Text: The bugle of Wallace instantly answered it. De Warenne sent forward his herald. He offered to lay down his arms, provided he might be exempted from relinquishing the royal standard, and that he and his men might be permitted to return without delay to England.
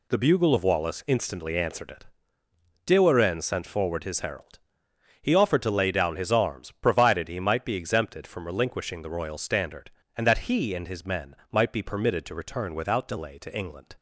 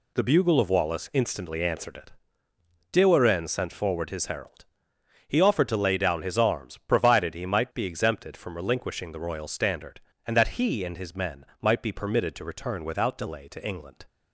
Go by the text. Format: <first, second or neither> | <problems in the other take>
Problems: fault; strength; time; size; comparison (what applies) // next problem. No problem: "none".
neither | pauses between "men" and "might"; slight; the same in both